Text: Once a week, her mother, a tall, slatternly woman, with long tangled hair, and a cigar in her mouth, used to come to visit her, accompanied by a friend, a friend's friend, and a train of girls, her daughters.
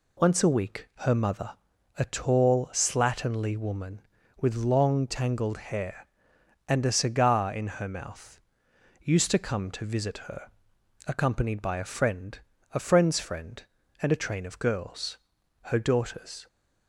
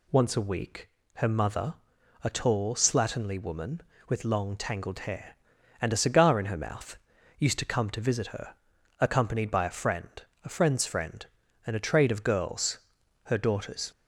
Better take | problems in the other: first | says "trade" for "train"; at 11.8 s

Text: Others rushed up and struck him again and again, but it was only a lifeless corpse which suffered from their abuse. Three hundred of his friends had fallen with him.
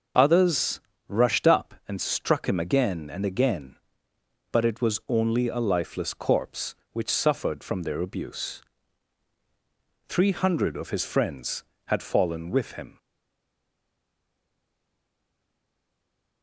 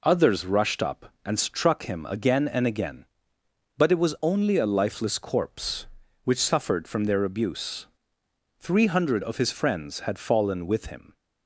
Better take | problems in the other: second | starts louder than the rest; until 1.4 s; 6.5 dB // pauses between "Others" and "rushed"; slight; at 0.8 s; 0.28 s long // stays silent after the last word; strong; from 12.9 s on; 3.5 s long

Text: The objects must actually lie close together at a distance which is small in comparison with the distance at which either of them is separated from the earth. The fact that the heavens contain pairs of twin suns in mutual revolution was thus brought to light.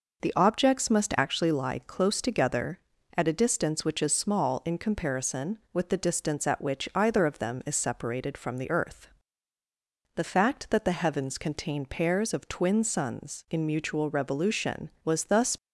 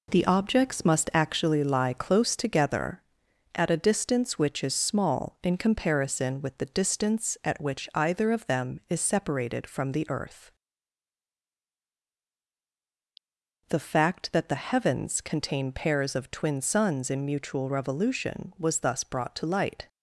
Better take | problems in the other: second | stops before "brought to light"; at 15.5 s

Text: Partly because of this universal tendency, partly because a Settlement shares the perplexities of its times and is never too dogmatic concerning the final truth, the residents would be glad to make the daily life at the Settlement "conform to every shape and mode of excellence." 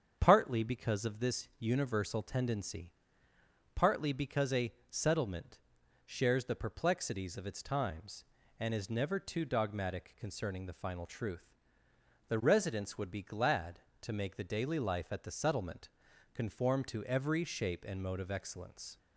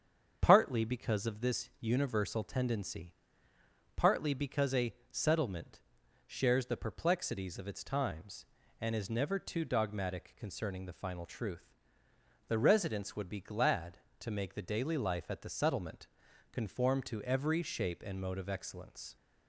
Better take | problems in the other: neither | starts louder than the rest; strong; the same in both // pauses between "a" and "Settlement"; slight; the same in both // pauses between "Settlement" and "shares"; noticeable; the same in both // pauses between "Settlement" and "conform"; noticeable; the same in both

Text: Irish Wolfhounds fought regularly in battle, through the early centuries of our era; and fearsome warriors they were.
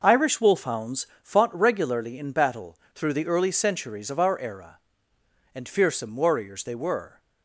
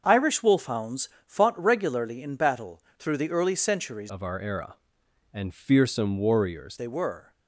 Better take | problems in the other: first | starts louder than the rest; until 1.0 s; 6.5 dB // pauses between "Wolfhounds" and "fought"; slight; at 1.0 s; 0.18 s long; slight in the first // changes voice from "of" to "warriors"; from 4.0 to 6.7 s; 2.7 s long

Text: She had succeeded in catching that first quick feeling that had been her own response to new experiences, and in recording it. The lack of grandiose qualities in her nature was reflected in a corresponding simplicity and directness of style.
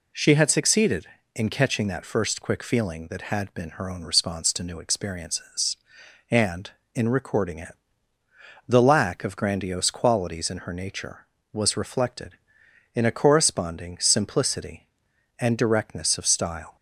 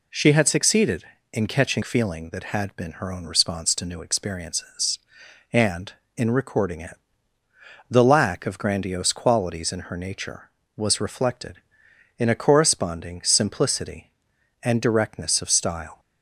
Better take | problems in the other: first | skips "that first quick"; at 1.8 s

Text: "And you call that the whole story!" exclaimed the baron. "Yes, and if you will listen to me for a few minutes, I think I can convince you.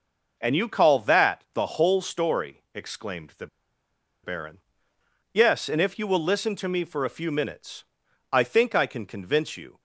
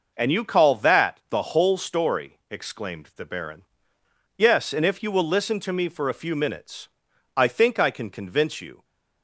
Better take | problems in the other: second | pauses between "the" and "baron"; noticeable; at 3.4 s; 0.75 s long

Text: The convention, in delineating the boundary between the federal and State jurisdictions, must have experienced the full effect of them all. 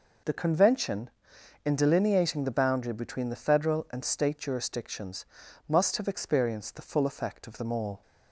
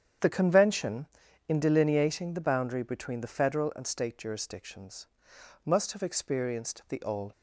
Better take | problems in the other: first | starts louder than the rest; strong; until 1.6 s; 8.5 dB // skips "full effect of them"; at 7.0 s

